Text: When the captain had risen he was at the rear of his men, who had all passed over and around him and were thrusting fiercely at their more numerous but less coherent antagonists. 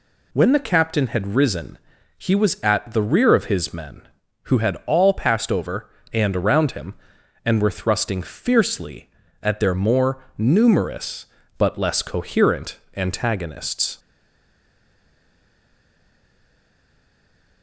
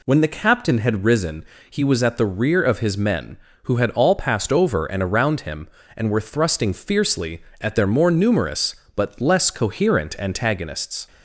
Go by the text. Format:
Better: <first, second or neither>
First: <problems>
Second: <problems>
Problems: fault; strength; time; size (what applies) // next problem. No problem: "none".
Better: second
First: pauses between "risen" and "he"; at 1.7 s; 0.42 s long // pauses between "more" and "numerous"; slight; at 10.2 s; 0.16 s long // pauses between "coherent" and "antagonists"; slight; at 12.7 s; 0.20 s long // stays silent after the last word; strong; from 13.9 s on; 3.7 s long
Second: pauses between "risen" and "he"; slight; at 1.4 s; 0.26 s long